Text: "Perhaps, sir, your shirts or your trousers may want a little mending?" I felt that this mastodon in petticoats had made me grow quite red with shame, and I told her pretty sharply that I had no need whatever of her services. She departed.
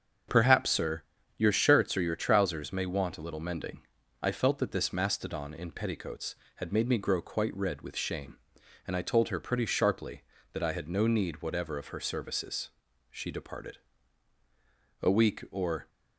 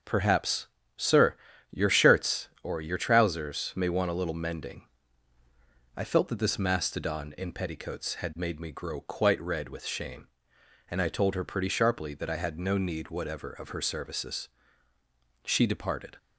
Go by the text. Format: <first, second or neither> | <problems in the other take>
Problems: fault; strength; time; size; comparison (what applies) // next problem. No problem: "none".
second | starts louder than the rest; strong; until 1.6 s; 7.5 dB; also in the second // goes on to say "A week or"; noticeable; from 15.0 s on; 0.87 s long